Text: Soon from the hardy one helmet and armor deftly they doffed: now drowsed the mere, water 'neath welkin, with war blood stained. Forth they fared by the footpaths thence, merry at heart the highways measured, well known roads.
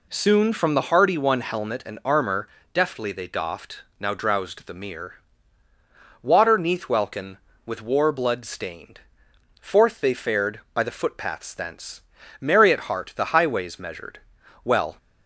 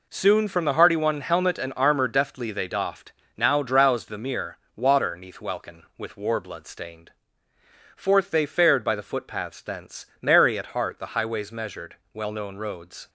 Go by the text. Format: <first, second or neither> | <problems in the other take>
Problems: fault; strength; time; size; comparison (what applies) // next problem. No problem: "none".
second | pauses between "armor" and "deftly"; slight; at 2.4 s; 0.26 s long // stops before "known roads"; at 14.9 s